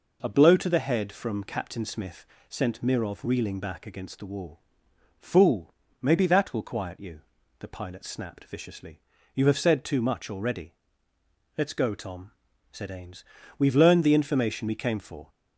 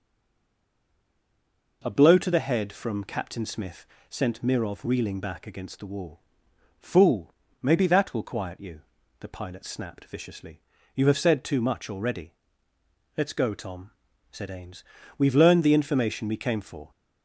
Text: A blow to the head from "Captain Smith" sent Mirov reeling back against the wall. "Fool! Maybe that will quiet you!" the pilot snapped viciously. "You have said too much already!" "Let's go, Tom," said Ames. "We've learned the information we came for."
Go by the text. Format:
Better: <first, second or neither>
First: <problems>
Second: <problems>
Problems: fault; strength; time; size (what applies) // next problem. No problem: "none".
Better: first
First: pauses between "Smith" and "sent"; slight; at 2.2 s; 0.20 s long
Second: stays silent before the first word; noticeable; until 1.8 s; 1.8 s long // pauses between "Smith" and "sent"; slight; at 3.8 s; 0.20 s long